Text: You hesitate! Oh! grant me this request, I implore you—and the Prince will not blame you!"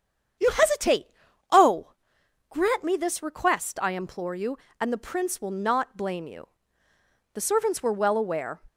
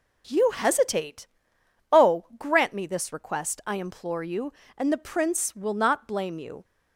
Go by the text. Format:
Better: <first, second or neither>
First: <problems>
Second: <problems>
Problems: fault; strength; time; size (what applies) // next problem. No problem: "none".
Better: second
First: starts louder than the rest; strong; until 1.8 s; 8.5 dB // goes on to say "The servants were well aware"; noticeable; from 7.3 s on; 1.3 s long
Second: none